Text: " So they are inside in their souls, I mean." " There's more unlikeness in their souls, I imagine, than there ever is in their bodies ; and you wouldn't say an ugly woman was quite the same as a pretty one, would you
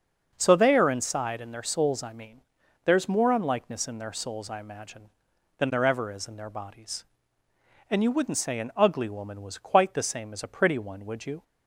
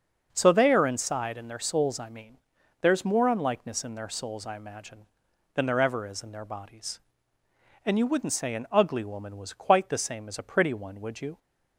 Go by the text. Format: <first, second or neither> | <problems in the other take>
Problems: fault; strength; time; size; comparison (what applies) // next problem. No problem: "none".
neither | starts louder than the rest; the same in both